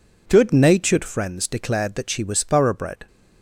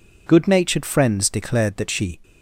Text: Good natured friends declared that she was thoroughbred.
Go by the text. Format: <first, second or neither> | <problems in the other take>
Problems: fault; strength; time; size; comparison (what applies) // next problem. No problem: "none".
first | stops before "was thoroughbred"; at 2.2 s